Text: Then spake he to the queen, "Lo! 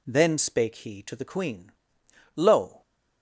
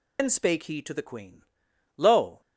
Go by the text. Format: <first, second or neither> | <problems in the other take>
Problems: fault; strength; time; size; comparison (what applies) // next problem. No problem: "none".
first | loses the start of "Then"; at 0.1 s; 90 ms